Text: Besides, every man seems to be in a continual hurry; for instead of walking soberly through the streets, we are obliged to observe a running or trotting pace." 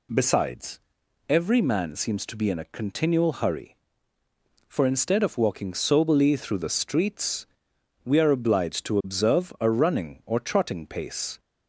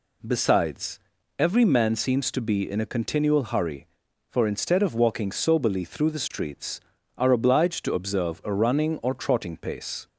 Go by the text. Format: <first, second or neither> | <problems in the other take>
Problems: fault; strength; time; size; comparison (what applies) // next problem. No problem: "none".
first | skips "we"; at 6.9 s